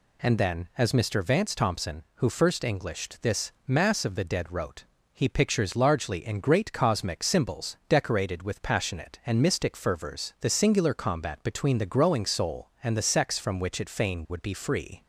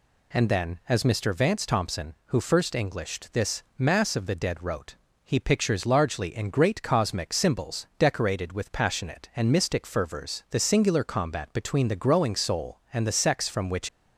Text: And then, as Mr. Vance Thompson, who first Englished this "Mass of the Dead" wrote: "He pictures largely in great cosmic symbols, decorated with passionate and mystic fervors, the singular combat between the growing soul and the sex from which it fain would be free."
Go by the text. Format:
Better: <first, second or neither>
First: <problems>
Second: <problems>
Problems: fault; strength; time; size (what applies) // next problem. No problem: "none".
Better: first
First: pauses between "this" and "Mass"; slight; at 3.5 s; 0.16 s long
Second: pauses between "this" and "Mass"; slight; at 3.6 s; 0.16 s long // stops before "it fain would be free"; at 13.8 s